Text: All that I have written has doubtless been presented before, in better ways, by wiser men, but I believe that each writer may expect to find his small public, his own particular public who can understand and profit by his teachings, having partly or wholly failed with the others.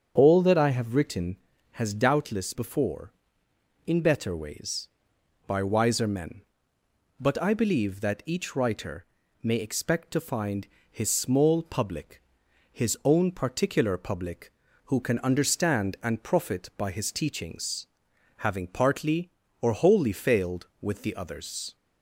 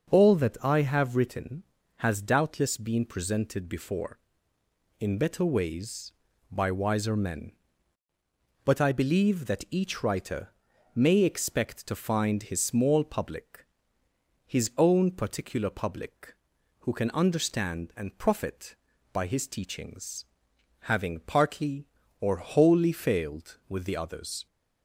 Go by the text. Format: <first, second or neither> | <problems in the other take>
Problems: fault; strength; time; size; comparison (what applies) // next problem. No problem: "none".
second | starts louder than the rest; strong; until 1.1 s; 7 dB; also in the second // skips "been presented"; at 2.5 s // pauses between "writer" and "may"; at 9.0 s; 0.38 s long; noticeable in the second // pauses between "find" and "his"; slight; at 10.6 s; 0.22 s long